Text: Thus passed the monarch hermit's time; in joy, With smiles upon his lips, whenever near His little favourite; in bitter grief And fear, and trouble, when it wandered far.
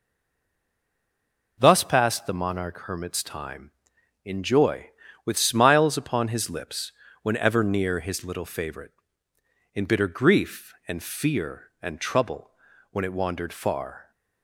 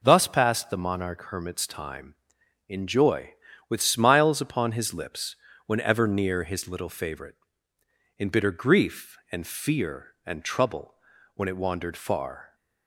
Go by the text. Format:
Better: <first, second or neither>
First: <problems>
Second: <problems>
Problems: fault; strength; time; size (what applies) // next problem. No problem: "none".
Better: second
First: stays silent before the first word; noticeable; until 1.5 s; 1.5 s long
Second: none